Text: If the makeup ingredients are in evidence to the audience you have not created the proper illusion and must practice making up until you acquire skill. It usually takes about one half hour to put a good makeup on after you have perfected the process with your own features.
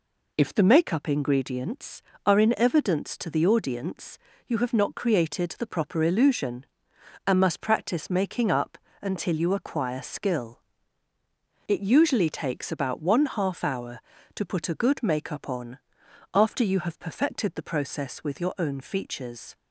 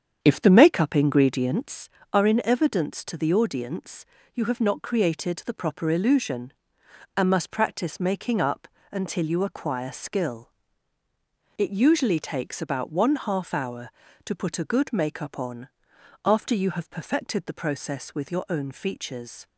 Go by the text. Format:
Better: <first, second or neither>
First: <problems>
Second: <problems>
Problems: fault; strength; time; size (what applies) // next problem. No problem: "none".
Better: first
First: pauses between "audience" and "you"; slight; at 4.1 s; 0.30 s long // pauses between "up" and "until"; slight; at 8.7 s; 0.24 s long // pauses between "on" and "after"; noticeable; at 15.7 s; 0.54 s long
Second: starts louder than the rest; strong; until 1.9 s; 8 dB // pauses between "audience" and "you"; slight; at 4.0 s; 0.30 s long // pauses between "up" and "until"; slight; at 8.6 s; 0.24 s long // pauses between "on" and "after"; noticeable; at 15.6 s; 0.56 s long